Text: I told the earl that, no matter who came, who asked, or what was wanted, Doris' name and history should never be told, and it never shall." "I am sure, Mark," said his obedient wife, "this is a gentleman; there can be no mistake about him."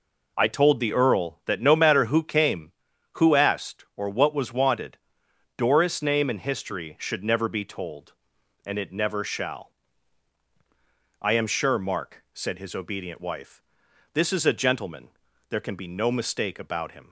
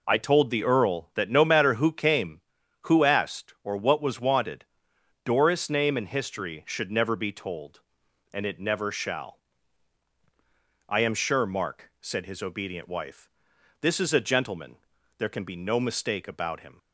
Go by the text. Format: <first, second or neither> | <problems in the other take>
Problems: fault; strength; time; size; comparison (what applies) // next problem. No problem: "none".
neither | none